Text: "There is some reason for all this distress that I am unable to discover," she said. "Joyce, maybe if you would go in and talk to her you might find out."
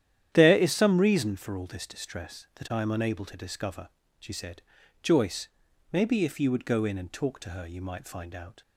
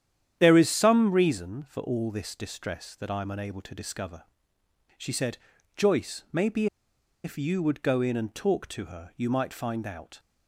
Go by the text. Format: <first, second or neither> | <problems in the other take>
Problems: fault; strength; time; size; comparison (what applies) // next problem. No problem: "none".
first | starts louder than the rest; strong; until 1.4 s; 10 dB; strong in the first // pauses between "maybe" and "if"; noticeable; at 6.6 s; 0.58 s long